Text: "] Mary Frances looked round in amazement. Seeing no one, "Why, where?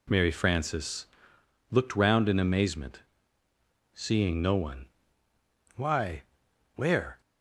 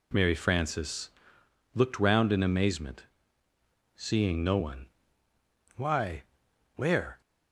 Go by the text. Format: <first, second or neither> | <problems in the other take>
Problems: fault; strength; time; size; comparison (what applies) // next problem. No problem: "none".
neither | pauses between "Frances" and "looked"; noticeable; the same in both